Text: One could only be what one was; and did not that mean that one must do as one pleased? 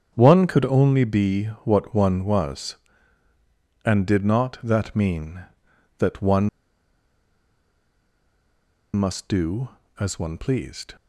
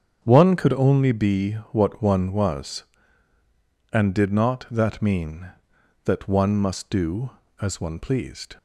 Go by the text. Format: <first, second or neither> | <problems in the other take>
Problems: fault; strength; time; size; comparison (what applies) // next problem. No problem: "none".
second | starts louder than the rest; strong; until 1.1 s; 8 dB; strong in the second // pauses between "be" and "what"; slight; at 1.4 s; 0.20 s long; slight in the second // pauses between "one" and "must"; strong; at 6.4 s; 2.4 s long